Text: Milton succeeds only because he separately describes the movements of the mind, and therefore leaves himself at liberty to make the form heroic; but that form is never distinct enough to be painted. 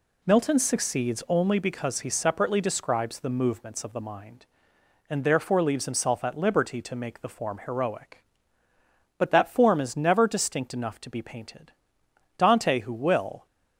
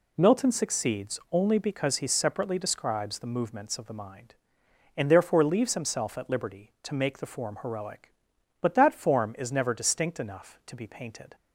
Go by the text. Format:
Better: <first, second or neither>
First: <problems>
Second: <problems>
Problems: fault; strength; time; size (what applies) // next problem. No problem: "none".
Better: second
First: goes on to say "Dante who will"; noticeable; from 12.3 s on; 1.1 s long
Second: none